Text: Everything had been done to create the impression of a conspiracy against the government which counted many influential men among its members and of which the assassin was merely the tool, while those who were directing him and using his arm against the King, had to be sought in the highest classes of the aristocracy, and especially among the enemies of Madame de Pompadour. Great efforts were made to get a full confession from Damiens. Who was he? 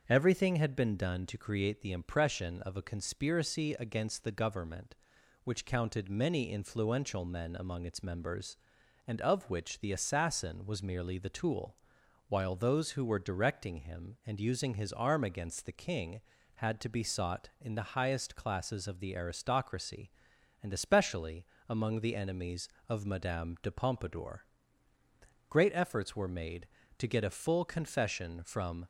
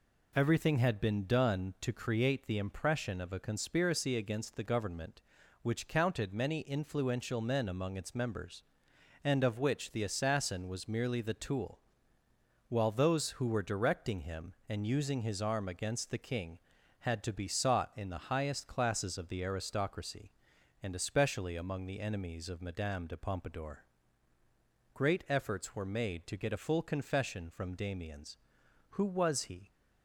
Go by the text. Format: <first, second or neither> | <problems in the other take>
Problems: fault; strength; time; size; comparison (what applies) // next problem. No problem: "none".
second | starts louder than the rest; until 1.0 s; 7 dB // pauses between "especially" and "among"; slight; at 21.4 s; 0.26 s long // stops before "Damiens Who was he"; at 28.8 s